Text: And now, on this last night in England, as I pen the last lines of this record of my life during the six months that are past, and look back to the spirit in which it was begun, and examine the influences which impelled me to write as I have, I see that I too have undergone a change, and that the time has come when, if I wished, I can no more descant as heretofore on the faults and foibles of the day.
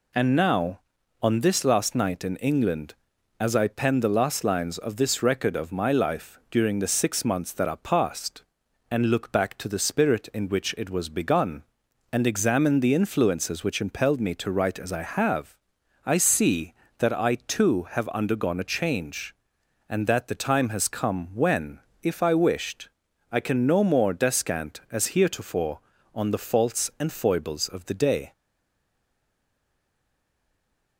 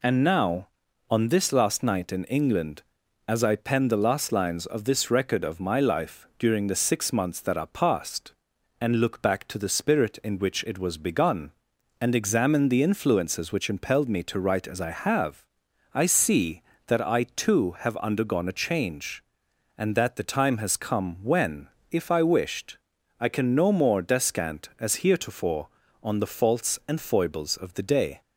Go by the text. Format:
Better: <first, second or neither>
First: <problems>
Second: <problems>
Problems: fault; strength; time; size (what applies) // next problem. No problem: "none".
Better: second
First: stays silent after the last word; strong; from 28.3 s on; 2.6 s long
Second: none